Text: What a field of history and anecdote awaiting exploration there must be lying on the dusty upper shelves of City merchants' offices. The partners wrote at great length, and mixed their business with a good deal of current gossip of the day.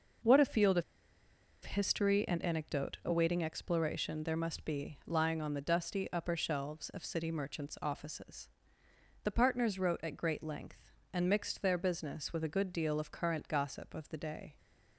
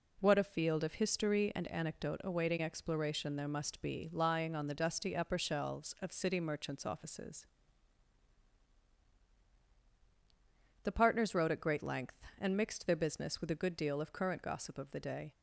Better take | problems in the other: second | pauses between "of" and "history"; noticeable; at 0.8 s; 0.81 s long

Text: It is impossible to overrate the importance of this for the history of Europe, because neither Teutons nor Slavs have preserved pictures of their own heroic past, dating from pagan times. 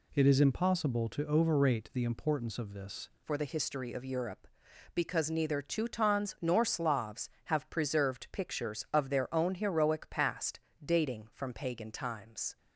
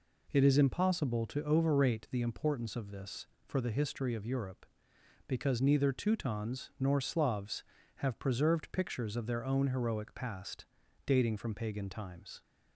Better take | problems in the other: second | changes voice at "for"; from 3.2 s on; 9.3 s long

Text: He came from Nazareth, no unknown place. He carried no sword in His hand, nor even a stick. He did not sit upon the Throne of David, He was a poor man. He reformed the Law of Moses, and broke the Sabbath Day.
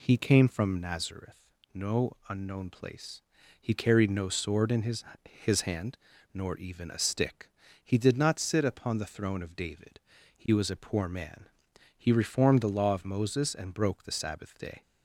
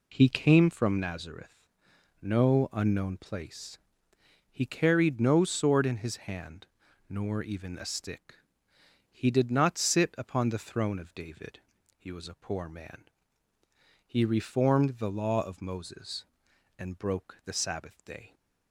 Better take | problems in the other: second | says "His" twice; at 5.2 s

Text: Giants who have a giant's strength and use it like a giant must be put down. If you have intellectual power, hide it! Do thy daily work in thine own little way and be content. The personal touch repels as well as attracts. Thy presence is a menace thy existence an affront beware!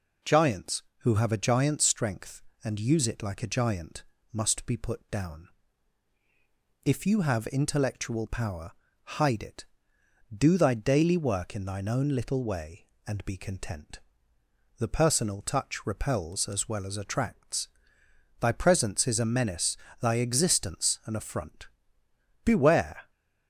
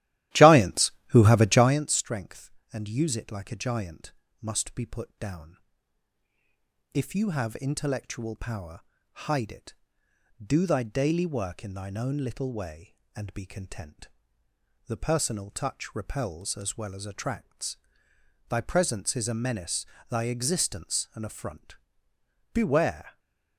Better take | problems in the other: first | starts louder than the rest; strong; until 1.8 s; 14.5 dB // pauses between "giant" and "must"; slight; at 4.1 s; 0.28 s long; slight in the first // pauses between "menace" and "thy"; slight; at 19.8 s; 0.24 s long; slight in the first // pauses between "affront" and "beware"; noticeable; at 21.7 s; 0.76 s long; noticeable in the first

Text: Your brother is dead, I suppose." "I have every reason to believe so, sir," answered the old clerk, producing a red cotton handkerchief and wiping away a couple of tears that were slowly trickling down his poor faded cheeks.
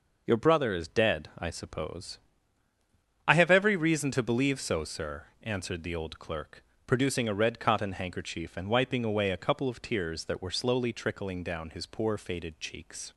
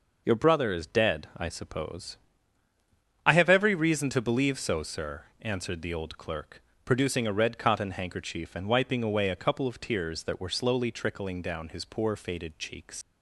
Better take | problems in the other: first | leaves "cheeks" unfinished; at 13.0 s; 105 ms

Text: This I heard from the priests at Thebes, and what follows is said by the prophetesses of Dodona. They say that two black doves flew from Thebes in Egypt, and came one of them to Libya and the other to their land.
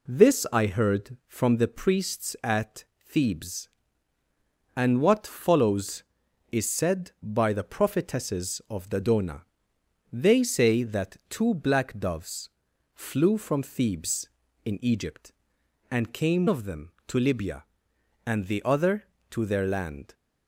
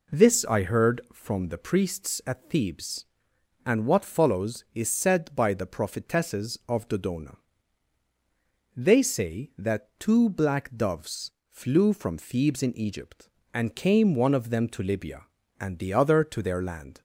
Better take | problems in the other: second | pauses between "at" and "Thebes"; slight; at 2.8 s; 0.24 s long // pauses between "doves" and "flew"; at 12.4 s; 0.44 s long; slight in the second // skips "one"; at 16.4 s

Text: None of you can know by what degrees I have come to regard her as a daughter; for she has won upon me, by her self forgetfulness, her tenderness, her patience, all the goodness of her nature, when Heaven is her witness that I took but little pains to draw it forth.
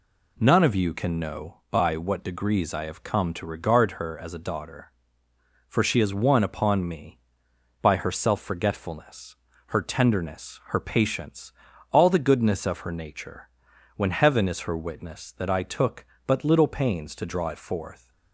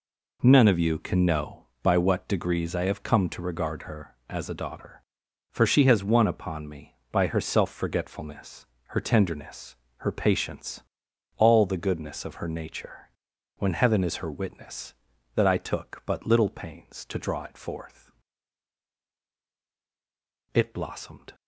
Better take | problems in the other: first | goes on to say "It blossomed"; noticeable; from 20.5 s on; 0.80 s long

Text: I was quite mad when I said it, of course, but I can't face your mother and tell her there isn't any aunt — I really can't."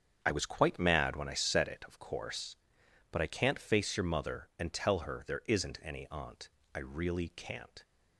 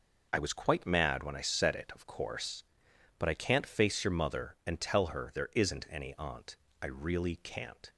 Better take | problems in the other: second | starts louder than the rest; strong; until 1.7 s; 8 dB

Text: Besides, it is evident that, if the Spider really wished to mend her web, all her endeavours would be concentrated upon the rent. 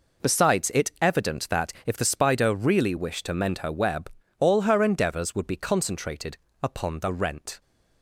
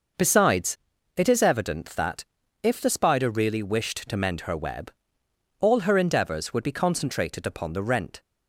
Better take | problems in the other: second | skips "is"; at 0.9 s // pauses between "concentrated" and "upon"; slight; at 6.3 s; 0.26 s long

